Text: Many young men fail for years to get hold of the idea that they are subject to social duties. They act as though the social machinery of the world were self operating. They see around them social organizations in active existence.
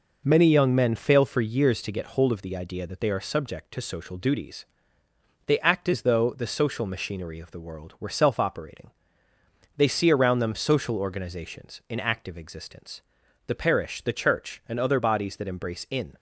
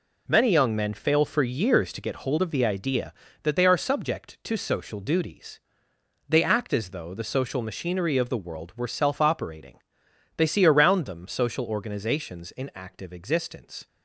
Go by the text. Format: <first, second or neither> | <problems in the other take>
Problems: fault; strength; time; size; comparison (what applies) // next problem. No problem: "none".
second | goes on to say "The parish the Church and other bodies that embrace in"; strong; from 13.4 s on; 2.6 s long